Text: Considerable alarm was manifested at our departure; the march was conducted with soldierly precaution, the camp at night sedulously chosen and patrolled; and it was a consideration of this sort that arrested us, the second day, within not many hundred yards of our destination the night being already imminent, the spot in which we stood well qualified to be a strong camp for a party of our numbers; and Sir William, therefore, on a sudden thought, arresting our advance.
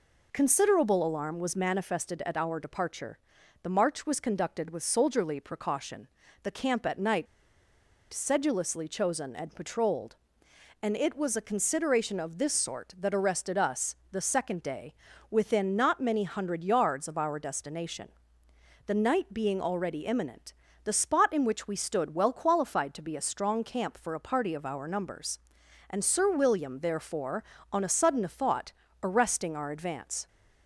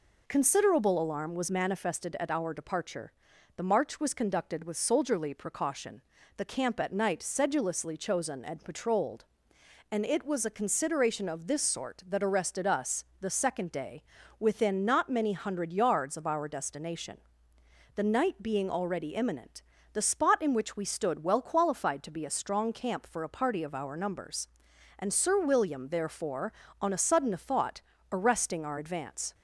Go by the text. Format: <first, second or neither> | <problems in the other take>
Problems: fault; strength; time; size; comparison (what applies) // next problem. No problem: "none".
second | pauses between "night" and "sedulously"; noticeable; at 7.2 s; 0.86 s long // pauses between "destination" and "the"; noticeable; at 18.0 s; 0.78 s long; noticeable in the second